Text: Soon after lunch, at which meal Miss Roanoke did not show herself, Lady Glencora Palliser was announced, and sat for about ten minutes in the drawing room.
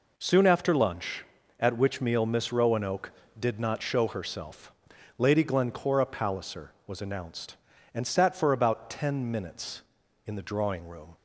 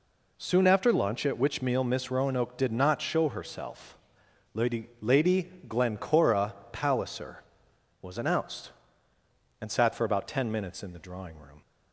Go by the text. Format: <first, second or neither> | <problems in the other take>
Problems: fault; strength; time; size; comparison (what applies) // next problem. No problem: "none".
first | says "Lady" twice; at 4.9 s // pauses between "Glencora" and "Palliser"; slight; at 6.5 s; 0.20 s long